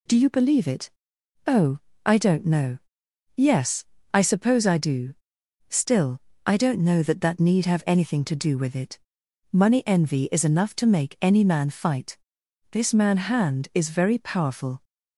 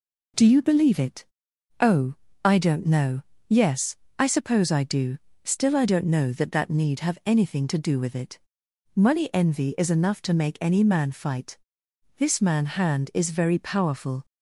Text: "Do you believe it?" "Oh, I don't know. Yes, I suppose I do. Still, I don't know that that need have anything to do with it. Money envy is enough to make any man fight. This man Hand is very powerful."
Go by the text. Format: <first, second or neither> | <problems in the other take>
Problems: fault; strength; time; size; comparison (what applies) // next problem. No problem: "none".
neither | none